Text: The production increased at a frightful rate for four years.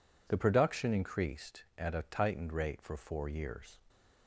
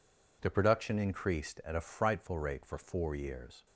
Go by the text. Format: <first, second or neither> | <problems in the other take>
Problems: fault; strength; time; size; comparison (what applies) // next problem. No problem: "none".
second | says "tightened" for "frightful"; at 2.0 s